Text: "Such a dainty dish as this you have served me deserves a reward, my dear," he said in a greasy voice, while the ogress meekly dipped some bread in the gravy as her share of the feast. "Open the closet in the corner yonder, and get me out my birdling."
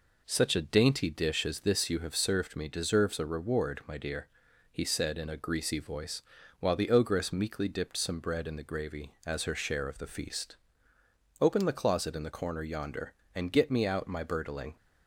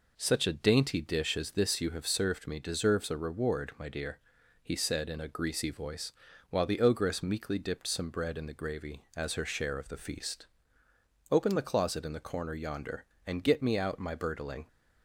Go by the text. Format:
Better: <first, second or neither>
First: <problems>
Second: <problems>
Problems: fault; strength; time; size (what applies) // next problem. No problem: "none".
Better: neither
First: none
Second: none